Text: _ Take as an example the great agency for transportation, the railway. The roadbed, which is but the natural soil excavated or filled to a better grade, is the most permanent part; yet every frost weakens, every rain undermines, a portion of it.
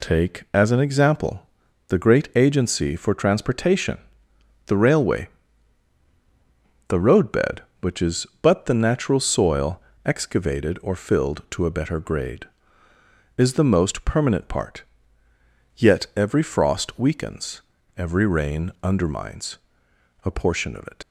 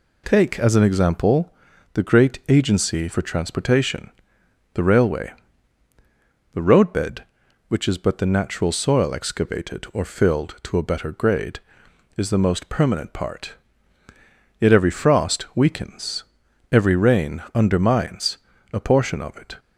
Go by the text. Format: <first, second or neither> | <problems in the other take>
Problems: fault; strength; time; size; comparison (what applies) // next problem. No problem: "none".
second | pauses between "example" and "the"; noticeable; at 1.4 s; 0.46 s long; also in the second // pauses between "soil" and "excavated"; slight; at 9.7 s; 0.24 s long // leaves "it" unfinished; at 21.0 s; 65 ms